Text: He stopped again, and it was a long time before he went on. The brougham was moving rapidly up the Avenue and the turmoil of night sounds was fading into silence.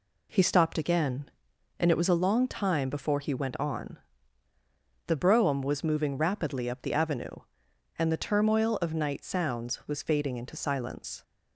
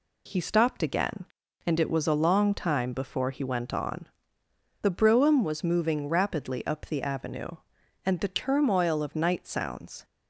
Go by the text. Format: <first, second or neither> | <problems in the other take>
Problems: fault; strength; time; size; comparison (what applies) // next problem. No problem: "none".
first | stops before "was fading into silence"; at 10.0 s